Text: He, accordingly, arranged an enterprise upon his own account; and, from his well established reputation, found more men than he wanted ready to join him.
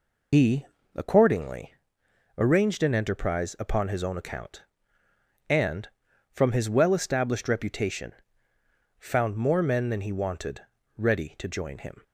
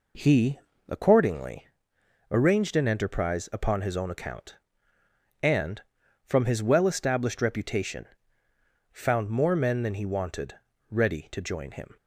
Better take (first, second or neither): second